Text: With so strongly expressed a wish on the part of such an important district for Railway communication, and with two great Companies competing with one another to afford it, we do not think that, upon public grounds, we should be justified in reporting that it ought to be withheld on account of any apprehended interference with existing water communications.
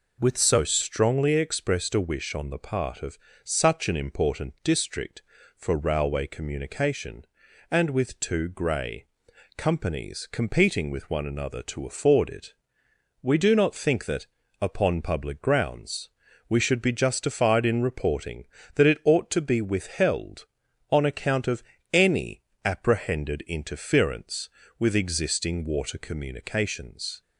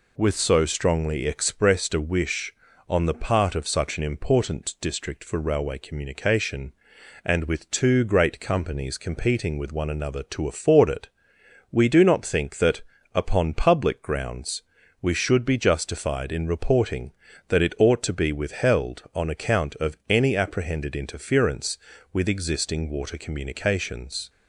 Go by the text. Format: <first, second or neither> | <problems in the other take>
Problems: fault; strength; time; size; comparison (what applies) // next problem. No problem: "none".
second | pauses between "of" and "such"; slight; at 3.1 s; 0.28 s long // says "grey" for "great"; at 8.4 s // pauses between "of" and "any"; slight; at 21.6 s; 0.32 s long // pauses between "any" and "apprehended"; slight; at 22.4 s; 0.22 s long